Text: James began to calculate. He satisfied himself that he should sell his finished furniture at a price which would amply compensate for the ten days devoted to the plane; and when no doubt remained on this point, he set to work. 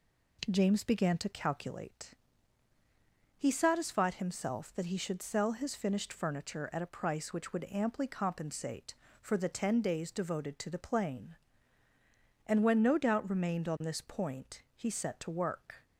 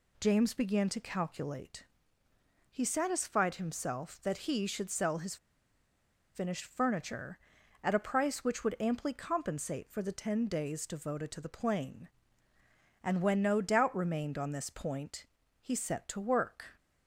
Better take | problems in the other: first | pauses between "his" and "finished"; at 5.3 s; 0.98 s long

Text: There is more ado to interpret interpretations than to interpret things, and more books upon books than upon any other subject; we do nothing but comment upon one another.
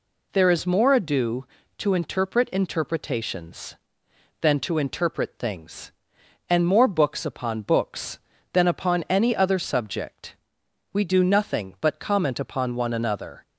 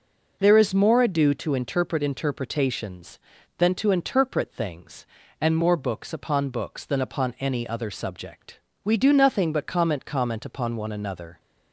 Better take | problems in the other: first | says "comment" twice; at 10.0 s

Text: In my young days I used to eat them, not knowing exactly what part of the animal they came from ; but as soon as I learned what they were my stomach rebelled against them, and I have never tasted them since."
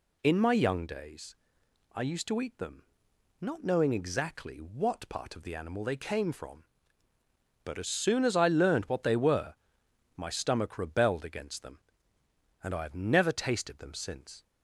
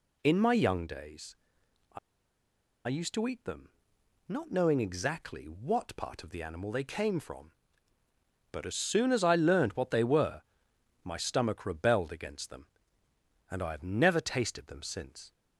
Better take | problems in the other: first | pauses between "days" and "I"; noticeable; at 1.3 s; 0.58 s long; noticeable in the first // pauses between "I" and "used"; noticeable; at 1.9 s; 0.88 s long // pauses between "were" and "my"; noticeable; at 10.4 s; 0.62 s long; noticeable in the first

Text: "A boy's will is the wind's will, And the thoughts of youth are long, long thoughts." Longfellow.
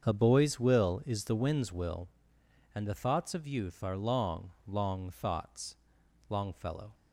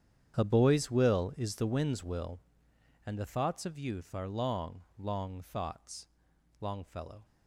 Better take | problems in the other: first | gets quieter; strong; throughout; 17 dB // starts louder than the rest; strong; until 1.4 s; 9 dB; also in the first

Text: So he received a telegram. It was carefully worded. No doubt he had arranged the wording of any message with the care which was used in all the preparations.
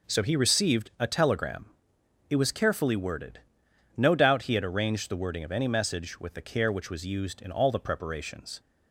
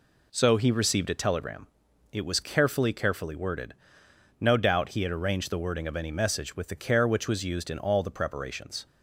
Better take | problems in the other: first | says "carefully" twice; at 2.9 s

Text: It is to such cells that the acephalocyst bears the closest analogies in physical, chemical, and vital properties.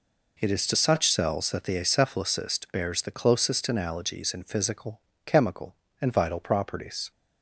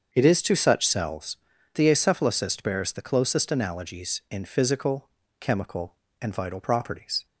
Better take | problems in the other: first | starts louder than the rest; until 1.1 s; 7 dB // skips "that"; at 1.5 s

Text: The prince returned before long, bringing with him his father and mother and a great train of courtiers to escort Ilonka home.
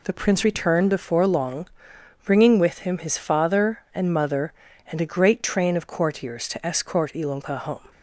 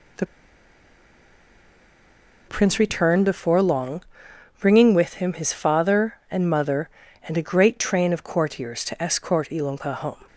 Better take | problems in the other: first | pauses between "The" and "prince"; strong; at 0.2 s; 2.2 s long

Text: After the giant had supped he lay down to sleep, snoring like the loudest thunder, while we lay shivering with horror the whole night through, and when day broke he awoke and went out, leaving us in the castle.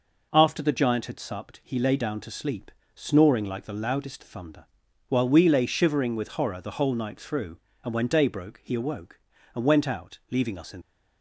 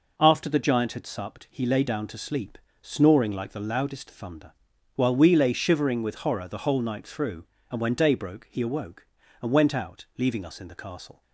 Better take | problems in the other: second | stops before "the castle"; at 10.8 s

